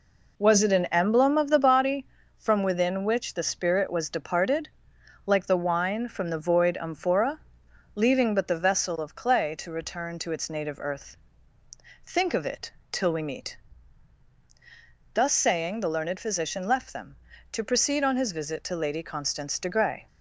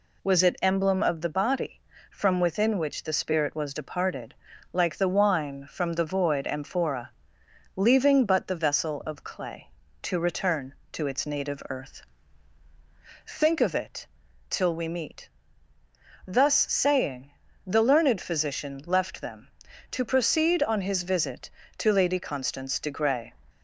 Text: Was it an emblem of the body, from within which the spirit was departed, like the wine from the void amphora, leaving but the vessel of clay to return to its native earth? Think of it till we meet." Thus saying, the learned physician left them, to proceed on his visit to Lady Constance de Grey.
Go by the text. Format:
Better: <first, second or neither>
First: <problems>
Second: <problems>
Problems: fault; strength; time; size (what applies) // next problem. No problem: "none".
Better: first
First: pauses between "it" and "till"; slight; at 12.7 s; 0.20 s long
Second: skips "an"; at 0.5 s // pauses between "it" and "till"; at 14.0 s; 0.42 s long